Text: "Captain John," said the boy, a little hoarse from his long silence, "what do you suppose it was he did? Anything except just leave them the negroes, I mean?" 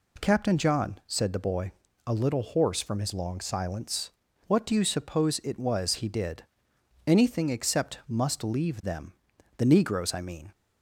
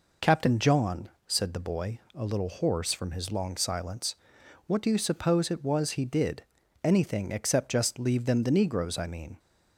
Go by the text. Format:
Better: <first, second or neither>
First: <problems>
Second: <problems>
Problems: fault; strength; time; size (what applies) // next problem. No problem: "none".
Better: second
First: says "must" for "just"; at 8.0 s // pauses between "them" and "the"; noticeable; at 9.1 s; 0.46 s long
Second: none